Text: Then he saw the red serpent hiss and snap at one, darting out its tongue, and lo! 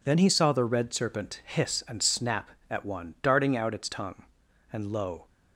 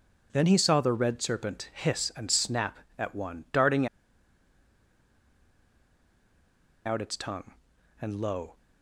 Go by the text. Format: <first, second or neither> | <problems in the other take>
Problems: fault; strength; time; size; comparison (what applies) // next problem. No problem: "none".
first | pauses between "darting" and "out"; strong; at 3.8 s; 2.9 s long